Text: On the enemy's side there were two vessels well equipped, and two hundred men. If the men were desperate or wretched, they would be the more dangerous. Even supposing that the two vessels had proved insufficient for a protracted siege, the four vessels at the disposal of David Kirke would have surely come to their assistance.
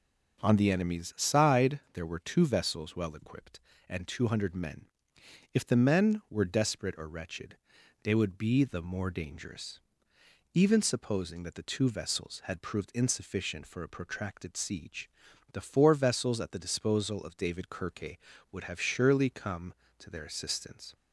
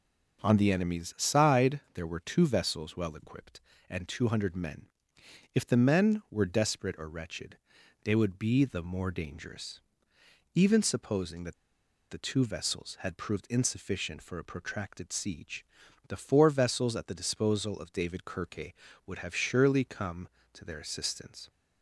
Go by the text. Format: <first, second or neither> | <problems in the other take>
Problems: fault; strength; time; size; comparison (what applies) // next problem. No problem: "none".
first | pauses between "that" and "the"; noticeable; at 11.5 s; 0.55 s long